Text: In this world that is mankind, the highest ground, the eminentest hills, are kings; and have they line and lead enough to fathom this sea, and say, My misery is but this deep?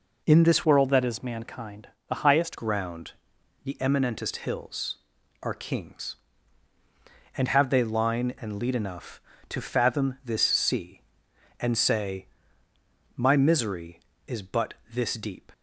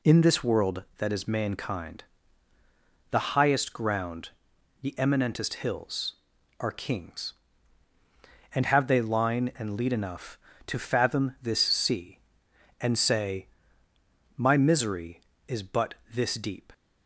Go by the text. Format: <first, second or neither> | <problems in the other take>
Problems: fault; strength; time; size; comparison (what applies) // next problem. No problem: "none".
second | changes voice from "world" to "highest"; from 0.6 to 2.5 s; 1.9 s long // pauses between "but" and "this"; slight; at 14.7 s; 0.18 s long; slight in the second